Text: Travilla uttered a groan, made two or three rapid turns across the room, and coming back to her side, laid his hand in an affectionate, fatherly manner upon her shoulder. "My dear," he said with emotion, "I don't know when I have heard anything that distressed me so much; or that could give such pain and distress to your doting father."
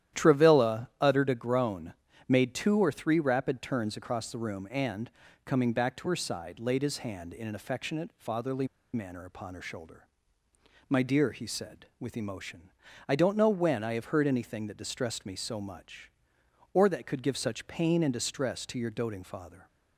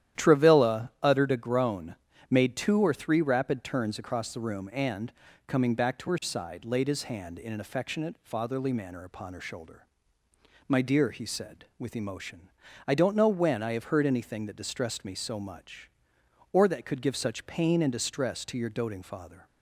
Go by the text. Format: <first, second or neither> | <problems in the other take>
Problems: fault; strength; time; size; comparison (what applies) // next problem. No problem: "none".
second | starts louder than the rest; strong; until 1.2 s; 11.5 dB; strong in the second // pauses between "and" and "coming"; slight; at 5.1 s; 0.34 s long; slight in the second // pauses between "fatherly" and "manner"; slight; at 8.6 s; 0.27 s long